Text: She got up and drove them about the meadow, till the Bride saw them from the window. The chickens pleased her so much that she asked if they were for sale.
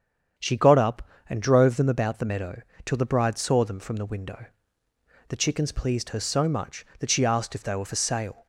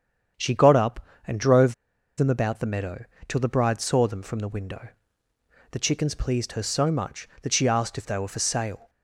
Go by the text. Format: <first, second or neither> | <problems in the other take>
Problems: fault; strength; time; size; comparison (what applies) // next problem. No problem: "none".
first | starts louder than the rest; strong; until 1.6 s; 8 dB; strong in the first // pauses between "drove" and "them"; at 1.7 s; 0.43 s long